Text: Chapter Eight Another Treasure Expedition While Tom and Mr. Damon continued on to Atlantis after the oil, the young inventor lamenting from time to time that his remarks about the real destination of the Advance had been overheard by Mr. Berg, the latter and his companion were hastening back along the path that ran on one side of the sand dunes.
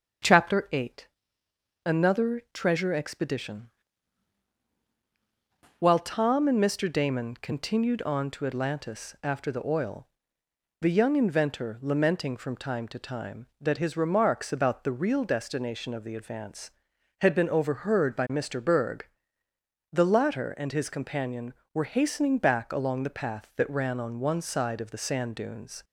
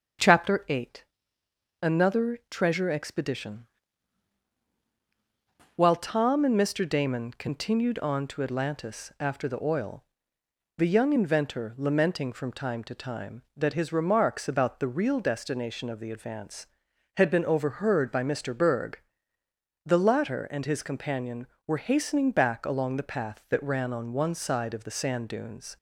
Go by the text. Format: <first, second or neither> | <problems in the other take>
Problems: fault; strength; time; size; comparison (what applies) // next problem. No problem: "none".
neither | starts louder than the rest; the same in both // pauses between "Eight" and "Another"; noticeable; the same in both // pauses between "Expedition" and "While"; strong; the same in both